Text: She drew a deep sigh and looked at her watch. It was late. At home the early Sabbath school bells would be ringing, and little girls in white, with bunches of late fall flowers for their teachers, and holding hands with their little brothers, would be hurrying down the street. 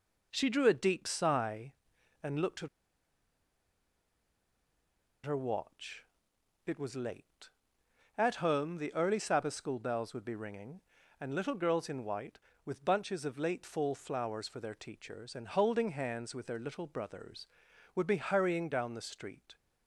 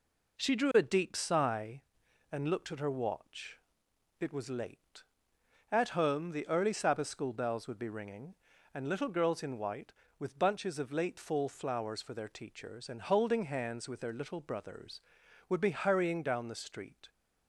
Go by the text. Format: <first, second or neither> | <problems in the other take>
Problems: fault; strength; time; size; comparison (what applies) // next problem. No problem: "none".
second | pauses between "at" and "her"; strong; at 2.6 s; 2.5 s long